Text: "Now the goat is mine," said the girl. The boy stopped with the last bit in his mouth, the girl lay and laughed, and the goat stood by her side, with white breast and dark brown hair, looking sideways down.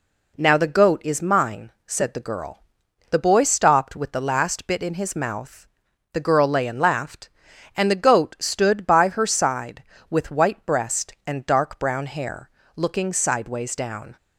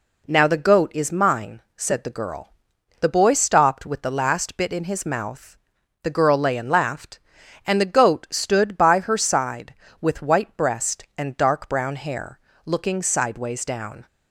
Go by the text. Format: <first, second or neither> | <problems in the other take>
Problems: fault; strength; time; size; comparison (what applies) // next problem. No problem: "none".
neither | none